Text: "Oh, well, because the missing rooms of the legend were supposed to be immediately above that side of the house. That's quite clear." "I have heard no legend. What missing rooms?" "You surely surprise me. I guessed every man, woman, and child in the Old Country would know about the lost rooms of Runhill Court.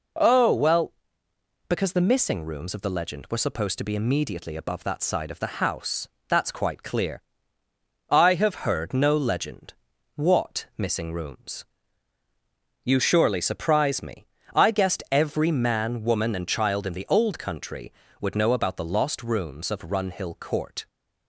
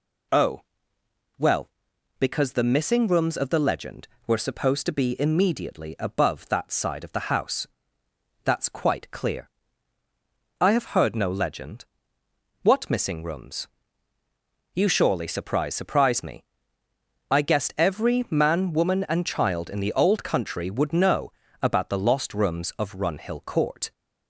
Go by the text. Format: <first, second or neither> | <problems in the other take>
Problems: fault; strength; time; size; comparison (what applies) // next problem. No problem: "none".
first | says "surprise" twice; at 15.7 s // pauses between "know" and "about"; slight; at 21.3 s; 0.30 s long